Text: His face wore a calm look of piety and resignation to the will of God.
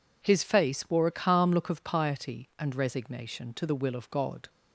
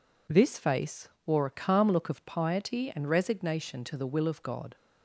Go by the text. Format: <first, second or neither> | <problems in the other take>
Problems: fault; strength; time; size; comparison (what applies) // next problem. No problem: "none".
first | says "This" for "His"; at 0.2 s // pauses between "face" and "wore"; slight; at 1.0 s; 0.18 s long